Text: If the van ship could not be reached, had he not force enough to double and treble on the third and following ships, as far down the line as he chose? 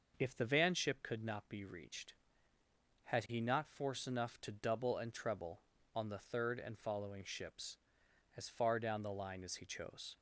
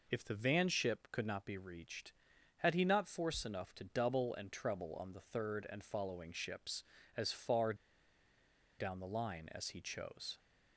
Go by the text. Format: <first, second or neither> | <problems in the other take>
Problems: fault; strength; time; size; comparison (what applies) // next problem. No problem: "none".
first | pauses between "far" and "down"; at 7.7 s; 1.0 s long